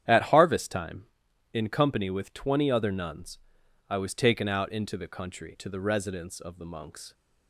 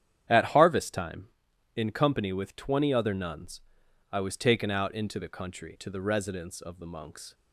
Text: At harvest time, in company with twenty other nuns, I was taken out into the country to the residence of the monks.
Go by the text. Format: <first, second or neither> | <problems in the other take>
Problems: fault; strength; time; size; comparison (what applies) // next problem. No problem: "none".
neither | starts louder than the rest; strong; the same in both